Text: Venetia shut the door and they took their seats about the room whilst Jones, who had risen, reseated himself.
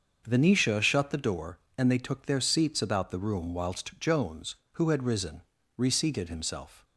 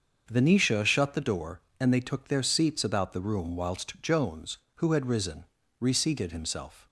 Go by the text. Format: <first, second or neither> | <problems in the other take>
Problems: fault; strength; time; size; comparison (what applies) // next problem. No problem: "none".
neither | starts louder than the rest; the same in both